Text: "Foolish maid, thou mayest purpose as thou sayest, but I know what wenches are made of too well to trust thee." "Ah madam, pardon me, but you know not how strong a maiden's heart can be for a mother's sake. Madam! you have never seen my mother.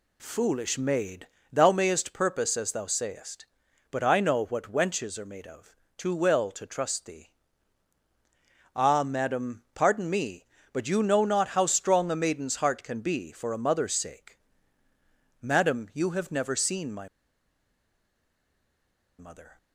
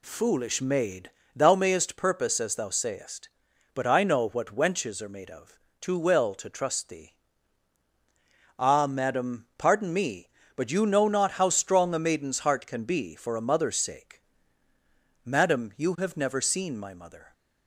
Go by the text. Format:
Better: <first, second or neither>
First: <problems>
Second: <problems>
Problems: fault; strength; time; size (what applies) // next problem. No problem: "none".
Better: second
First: pauses between "of" and "too"; slight; at 5.7 s; 0.22 s long // pauses between "my" and "mother"; strong; at 17.0 s; 2.1 s long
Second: pauses between "of" and "too"; slight; at 5.5 s; 0.22 s long